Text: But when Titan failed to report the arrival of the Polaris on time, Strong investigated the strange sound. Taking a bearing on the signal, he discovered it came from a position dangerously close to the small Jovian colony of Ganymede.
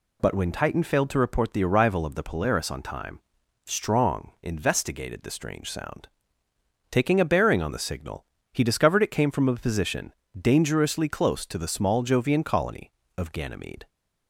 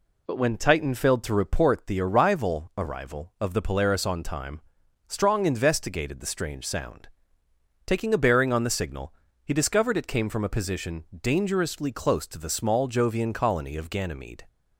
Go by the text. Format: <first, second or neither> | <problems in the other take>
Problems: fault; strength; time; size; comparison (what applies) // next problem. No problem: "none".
first | says "arrival" twice; at 2.7 s // pauses between "position" and "dangerously"; slight; at 11.0 s; 0.18 s long; slight in the first